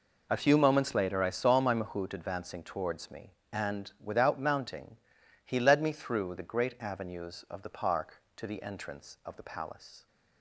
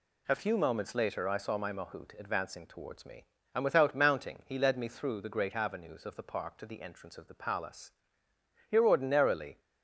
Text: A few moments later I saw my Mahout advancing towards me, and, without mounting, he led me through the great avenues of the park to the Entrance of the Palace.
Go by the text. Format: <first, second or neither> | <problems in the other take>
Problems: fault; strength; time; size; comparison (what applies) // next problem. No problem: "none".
first | goes on to say "Here ordinarily"; noticeable; from 8.7 s on; 0.88 s long